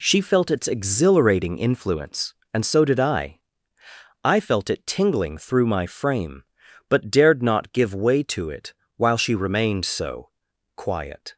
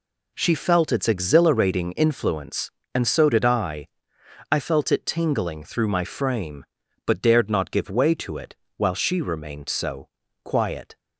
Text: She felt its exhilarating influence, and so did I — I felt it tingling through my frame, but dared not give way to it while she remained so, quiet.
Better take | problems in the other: neither | pauses between "it" and "while"; slight; the same in both

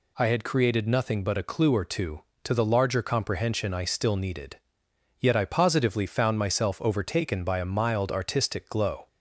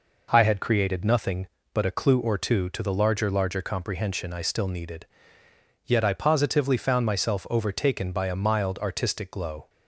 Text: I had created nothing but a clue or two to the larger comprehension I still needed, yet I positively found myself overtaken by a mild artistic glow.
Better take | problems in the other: first | says "larger" twice; at 3.3 s

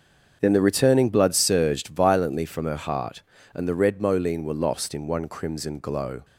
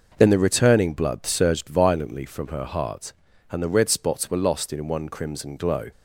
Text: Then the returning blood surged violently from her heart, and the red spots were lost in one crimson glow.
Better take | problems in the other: second | starts louder than the rest; until 1.4 s; 7 dB // says "moline" for "spots"; at 4.0 s

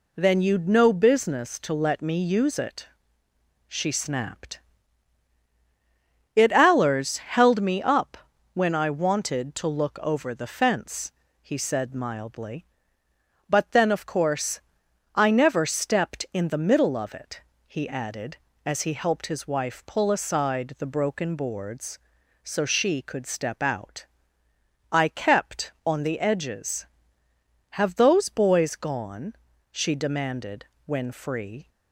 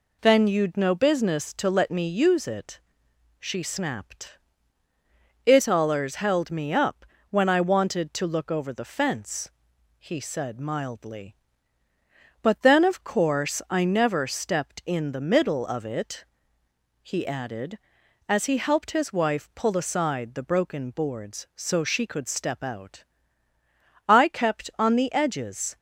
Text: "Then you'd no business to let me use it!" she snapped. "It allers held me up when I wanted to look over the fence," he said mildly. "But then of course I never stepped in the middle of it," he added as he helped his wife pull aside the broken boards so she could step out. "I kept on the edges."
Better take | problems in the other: second | pauses between "up" and "when"; slight; at 8.1 s; 0.36 s long; slight in the second // pauses between "course" and "I"; noticeable; at 14.6 s; 0.54 s long // goes on to say "Have those boys gone she demanded when free"; strong; from 27.7 s on; 3.9 s long

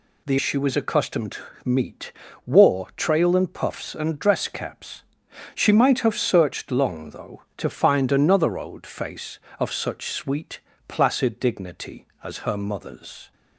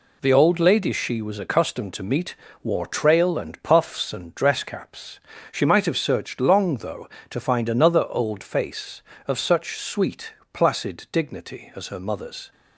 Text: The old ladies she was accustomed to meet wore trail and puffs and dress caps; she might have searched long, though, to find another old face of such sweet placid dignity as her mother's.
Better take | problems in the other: second | skips "old ladies"; at 0.3 s // pauses between "to" and "meet"; slight; at 1.4 s; 0.24 s long // pauses between "meet" and "wore"; slight; at 2.1 s; 0.34 s long; slight in the second // pauses between "sweet" and "placid"; slight; at 10.5 s; 0.26 s long; slight in the second

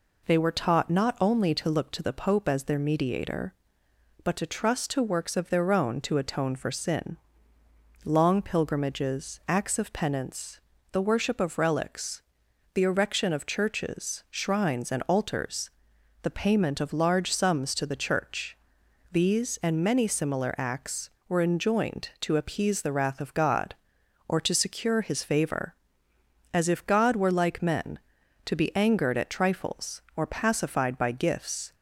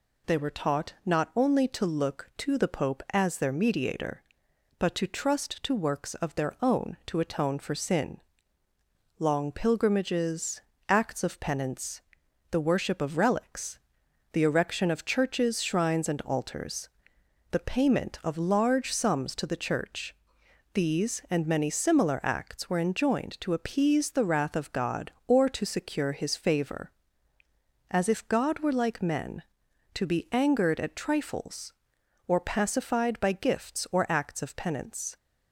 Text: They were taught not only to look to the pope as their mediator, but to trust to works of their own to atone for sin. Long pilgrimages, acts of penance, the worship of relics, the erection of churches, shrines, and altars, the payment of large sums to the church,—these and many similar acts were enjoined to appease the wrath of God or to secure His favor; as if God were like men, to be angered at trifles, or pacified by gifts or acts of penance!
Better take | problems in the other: second | stops before "or acts of penance"; at 31.7 s

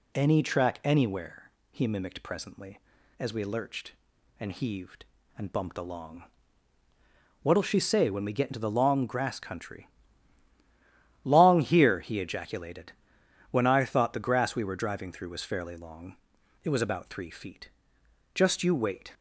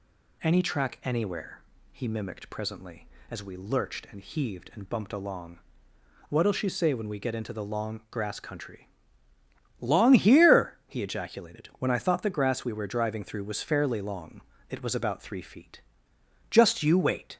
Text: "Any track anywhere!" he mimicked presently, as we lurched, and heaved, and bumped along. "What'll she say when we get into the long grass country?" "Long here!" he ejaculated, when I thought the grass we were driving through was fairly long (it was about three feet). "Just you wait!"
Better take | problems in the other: neither | none

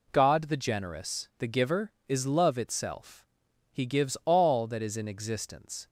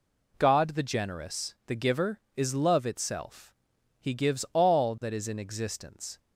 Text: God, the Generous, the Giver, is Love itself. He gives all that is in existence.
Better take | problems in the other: neither | none

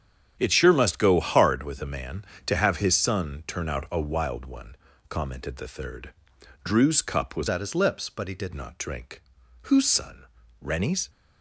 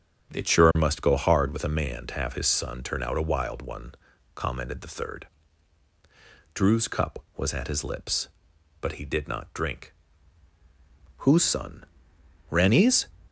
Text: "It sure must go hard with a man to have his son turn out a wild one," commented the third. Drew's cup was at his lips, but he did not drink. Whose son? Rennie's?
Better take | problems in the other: second | starts louder than the rest; strong; until 1.3 s; 8.5 dB; strong in the second // changes voice from "at" to "did"; from 7.4 to 8.5 s; 1.1 s long

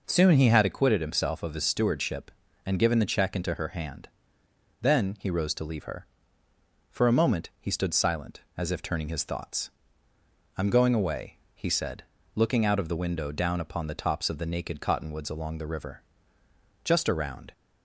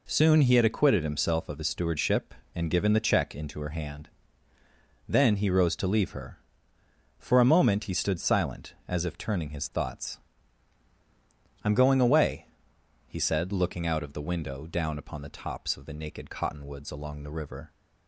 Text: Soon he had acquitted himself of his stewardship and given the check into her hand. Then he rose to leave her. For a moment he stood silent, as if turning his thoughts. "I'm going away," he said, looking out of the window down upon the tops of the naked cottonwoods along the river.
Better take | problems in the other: second | goes on to say "Just around"; noticeable; from 16.8 s on; 0.68 s long

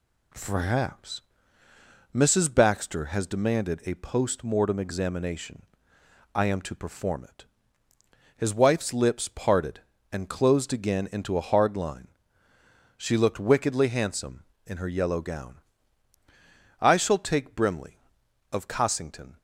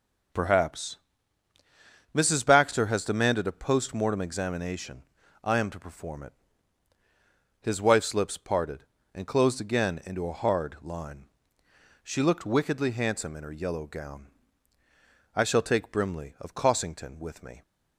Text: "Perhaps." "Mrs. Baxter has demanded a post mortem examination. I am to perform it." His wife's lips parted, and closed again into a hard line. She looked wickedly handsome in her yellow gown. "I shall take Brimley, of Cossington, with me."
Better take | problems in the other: second | stops before "with me"; at 19.3 s

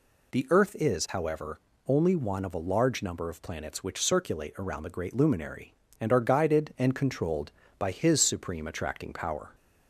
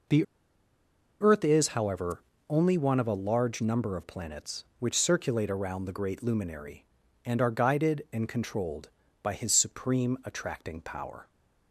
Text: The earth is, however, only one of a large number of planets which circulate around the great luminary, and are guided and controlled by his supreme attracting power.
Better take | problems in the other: first | pauses between "The" and "earth"; noticeable; at 0.2 s; 0.96 s long

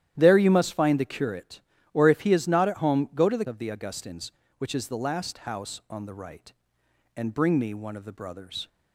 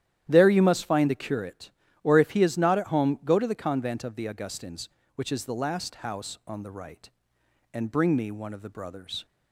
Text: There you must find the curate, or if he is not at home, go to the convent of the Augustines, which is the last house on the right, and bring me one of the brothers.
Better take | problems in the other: second | starts louder than the rest; strong; until 1.1 s; 11.5 dB; strong in the second // skips "convent"; at 3.4 s

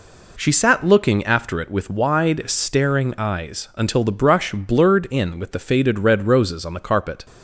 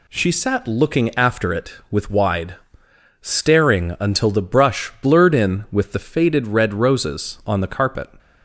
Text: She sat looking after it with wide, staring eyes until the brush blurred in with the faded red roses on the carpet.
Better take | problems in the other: first | skips "eyes"; at 3.9 s

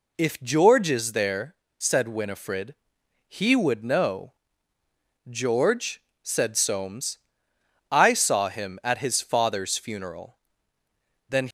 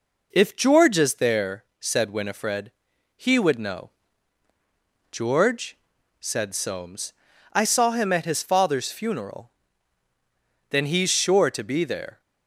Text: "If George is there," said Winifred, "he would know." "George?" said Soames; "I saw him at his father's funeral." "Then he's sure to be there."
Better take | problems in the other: second | stops before "he's sure to be there"; at 11.4 s

